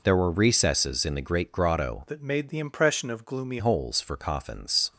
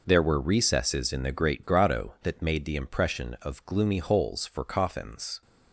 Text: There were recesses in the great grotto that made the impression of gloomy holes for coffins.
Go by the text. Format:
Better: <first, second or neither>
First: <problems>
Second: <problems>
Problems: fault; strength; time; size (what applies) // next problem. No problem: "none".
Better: second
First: changes voice from "that" to "gloomy"; from 2.0 to 3.5 s; 1.5 s long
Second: none